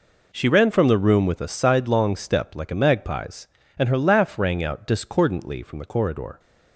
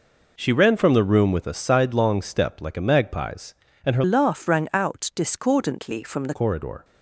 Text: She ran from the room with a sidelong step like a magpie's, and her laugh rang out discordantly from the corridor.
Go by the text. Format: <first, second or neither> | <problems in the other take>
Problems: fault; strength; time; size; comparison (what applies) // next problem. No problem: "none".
first | changes voice from "laugh" to "the"; from 4.0 to 6.3 s; 2.3 s long